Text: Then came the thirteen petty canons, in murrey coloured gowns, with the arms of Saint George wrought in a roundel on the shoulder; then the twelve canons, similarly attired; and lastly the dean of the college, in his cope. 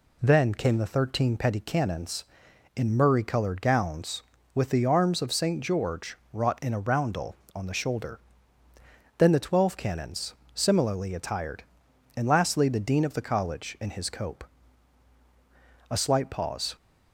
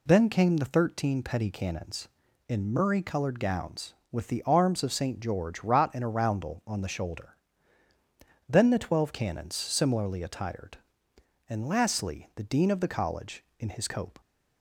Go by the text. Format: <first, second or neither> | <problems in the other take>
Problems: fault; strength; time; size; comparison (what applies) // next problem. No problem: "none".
second | pauses between "George" and "wrought"; slight; at 6.1 s; 0.16 s long // goes on to say "A slight pause"; noticeable; from 15.8 s on; 0.86 s long